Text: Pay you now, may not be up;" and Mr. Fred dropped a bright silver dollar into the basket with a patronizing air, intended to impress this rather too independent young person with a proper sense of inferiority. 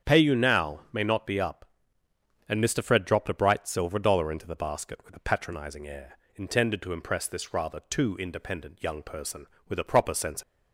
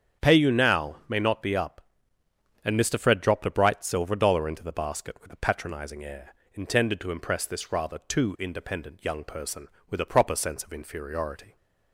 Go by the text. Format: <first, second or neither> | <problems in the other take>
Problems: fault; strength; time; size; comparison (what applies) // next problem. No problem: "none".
second | starts louder than the rest; strong; until 1.1 s; 8 dB; strong in the second // stops before "of inferiority"; at 10.4 s